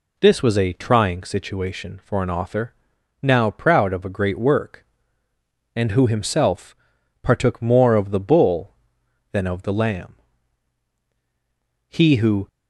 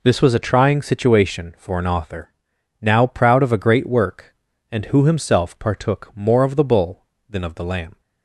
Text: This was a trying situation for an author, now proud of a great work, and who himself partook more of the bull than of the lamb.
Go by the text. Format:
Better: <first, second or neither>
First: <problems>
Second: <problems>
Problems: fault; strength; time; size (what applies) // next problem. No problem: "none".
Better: second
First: pauses between "himself" and "partook"; noticeable; at 6.7 s; 0.46 s long // goes on to say "He who"; from 11.8 s on; 0.60 s long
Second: none